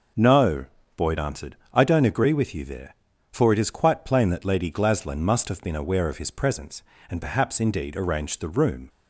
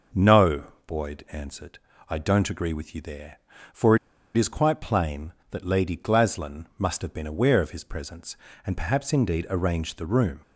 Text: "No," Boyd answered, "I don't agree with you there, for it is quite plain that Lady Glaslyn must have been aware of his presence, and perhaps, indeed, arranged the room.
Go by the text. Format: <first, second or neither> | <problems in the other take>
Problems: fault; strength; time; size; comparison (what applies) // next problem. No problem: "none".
first | pauses between "for" and "it"; at 3.9 s; 0.38 s long